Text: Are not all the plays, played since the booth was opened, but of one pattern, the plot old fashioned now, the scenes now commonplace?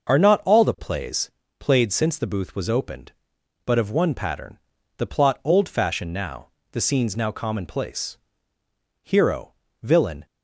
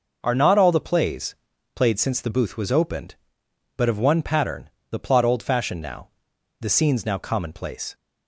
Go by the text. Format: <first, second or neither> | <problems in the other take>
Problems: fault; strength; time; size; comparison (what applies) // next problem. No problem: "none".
second | starts louder than the rest; noticeable; until 1.2 s; 6 dB // goes on to say "Hero villain"; noticeable; from 9.0 s on; 1.2 s long